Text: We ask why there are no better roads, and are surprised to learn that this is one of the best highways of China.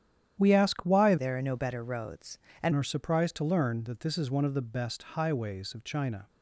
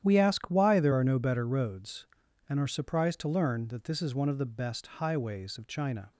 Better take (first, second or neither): second